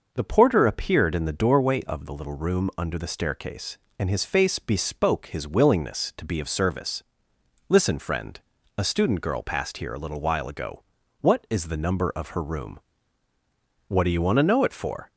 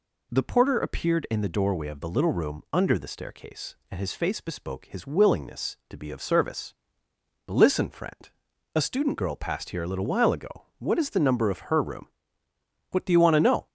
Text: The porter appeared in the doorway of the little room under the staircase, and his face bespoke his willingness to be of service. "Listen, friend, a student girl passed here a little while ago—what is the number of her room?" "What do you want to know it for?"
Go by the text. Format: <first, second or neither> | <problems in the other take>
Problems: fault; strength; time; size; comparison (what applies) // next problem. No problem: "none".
first | stops before "it for"; at 13.6 s